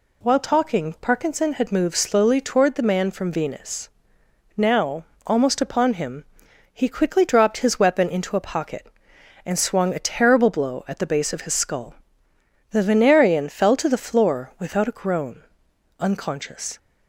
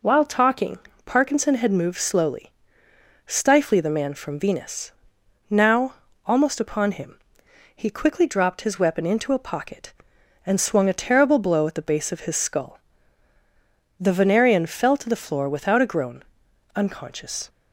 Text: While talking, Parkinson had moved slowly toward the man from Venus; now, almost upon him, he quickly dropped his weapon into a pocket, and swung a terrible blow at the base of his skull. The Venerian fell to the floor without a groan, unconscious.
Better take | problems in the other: first | says "stifly" for "toward"; at 3.2 s

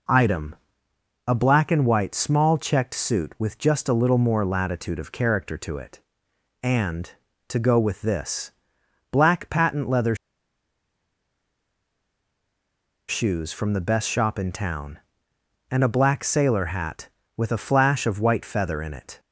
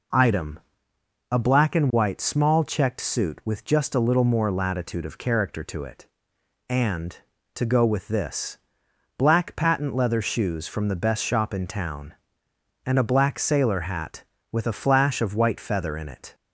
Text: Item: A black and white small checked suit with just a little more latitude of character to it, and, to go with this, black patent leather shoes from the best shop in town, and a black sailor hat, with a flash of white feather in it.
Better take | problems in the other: second | pauses between "leather" and "shoes"; strong; at 10.1 s; 2.9 s long

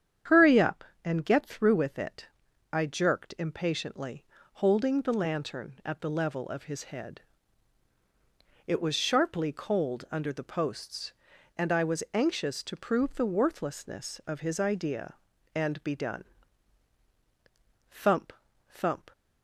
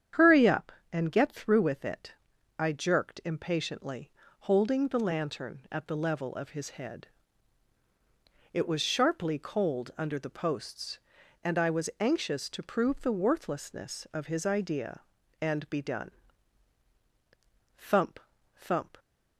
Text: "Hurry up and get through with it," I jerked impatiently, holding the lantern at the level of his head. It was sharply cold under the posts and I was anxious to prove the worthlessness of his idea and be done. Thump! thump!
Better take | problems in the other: neither | starts louder than the rest; strong; the same in both

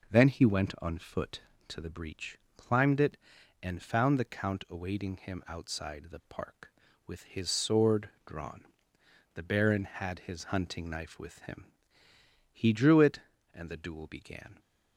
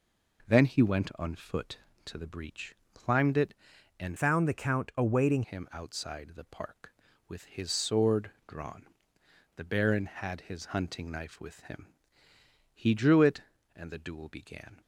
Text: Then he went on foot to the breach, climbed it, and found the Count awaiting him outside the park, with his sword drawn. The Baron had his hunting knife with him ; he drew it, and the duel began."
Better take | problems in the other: first | changes voice from "found" to "awaiting"; from 4.1 to 5.4 s; 1.3 s long // pauses between "sword" and "drawn"; slight; at 8.3 s; 0.16 s long; slight in the first

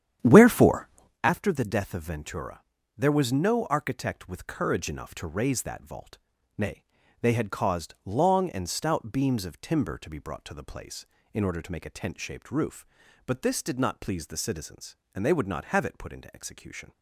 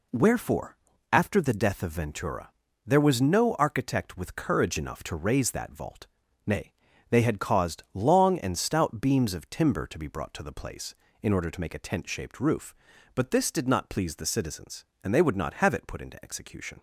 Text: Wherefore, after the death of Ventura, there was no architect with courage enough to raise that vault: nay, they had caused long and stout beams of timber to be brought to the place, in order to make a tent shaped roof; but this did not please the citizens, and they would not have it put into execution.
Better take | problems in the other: second | starts louder than the rest; strong; until 1.2 s; 9.5 dB

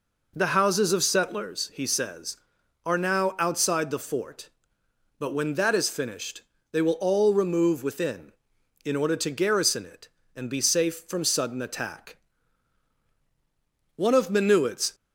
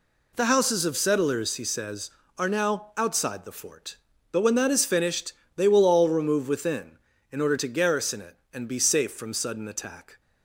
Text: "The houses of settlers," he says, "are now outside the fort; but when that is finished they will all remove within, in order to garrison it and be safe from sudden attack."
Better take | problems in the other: second | pauses between "finished" and "they"; slight; at 6.4 s; 0.30 s long; slight in the second // goes on to say "One of Minuit's"; noticeable; from 13.9 s on; 1.0 s long

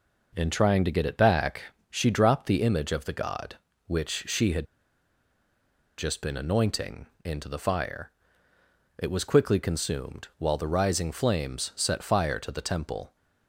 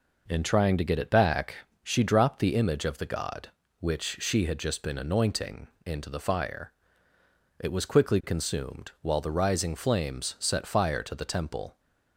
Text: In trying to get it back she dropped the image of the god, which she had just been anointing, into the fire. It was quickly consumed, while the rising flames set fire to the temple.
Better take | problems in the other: second | pauses between "back" and "she"; slight; at 1.6 s; 0.30 s long; slight in the second // pauses between "had" and "just"; strong; at 4.6 s; 1.3 s long

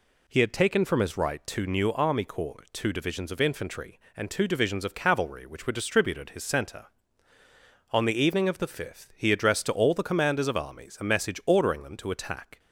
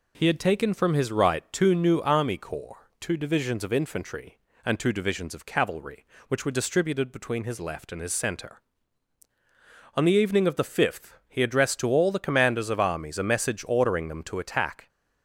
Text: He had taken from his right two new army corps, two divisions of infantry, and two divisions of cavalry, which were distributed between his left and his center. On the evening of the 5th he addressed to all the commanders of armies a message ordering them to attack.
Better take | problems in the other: second | skips "between his left and"; at 6.3 s

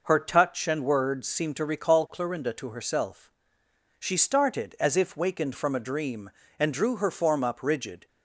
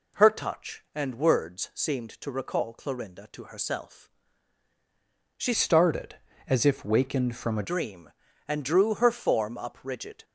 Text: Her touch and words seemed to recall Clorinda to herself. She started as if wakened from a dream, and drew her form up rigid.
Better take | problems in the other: first | changes voice from "started" to "a"; from 5.5 to 7.6 s; 2.1 s long

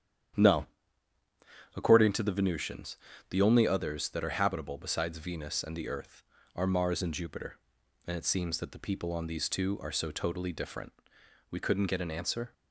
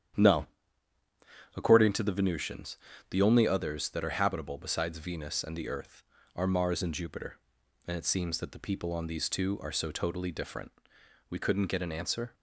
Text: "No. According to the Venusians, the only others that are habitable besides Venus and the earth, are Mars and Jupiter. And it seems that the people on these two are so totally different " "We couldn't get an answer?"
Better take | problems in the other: neither | starts louder than the rest; strong; the same in both

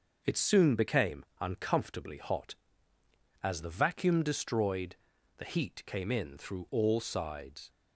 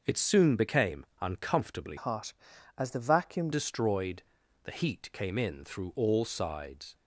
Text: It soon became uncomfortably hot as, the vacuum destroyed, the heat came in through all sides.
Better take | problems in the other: first | starts louder than the rest; noticeable; until 1.0 s; 6 dB // pauses between "became" and "uncomfortably"; slight; at 1.0 s; 0.16 s long; slight in the first // changes voice from "hot" to "vacuum"; from 1.9 to 3.5 s; 1.6 s long

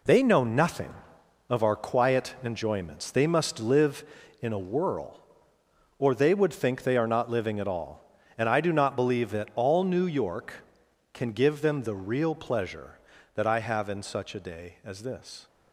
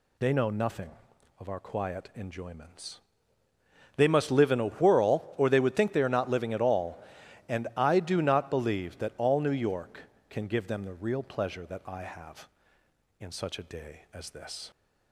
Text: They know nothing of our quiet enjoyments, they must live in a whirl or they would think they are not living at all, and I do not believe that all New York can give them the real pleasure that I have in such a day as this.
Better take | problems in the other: second | gets quieter; strong; throughout; 8.5 dB

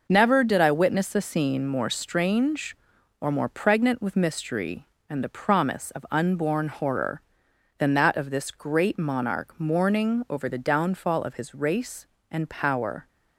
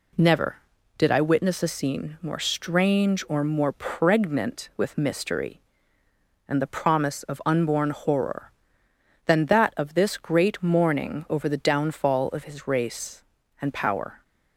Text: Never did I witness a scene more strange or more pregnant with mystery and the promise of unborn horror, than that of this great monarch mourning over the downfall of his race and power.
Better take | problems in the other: first | skips "monarch"; at 10.6 s

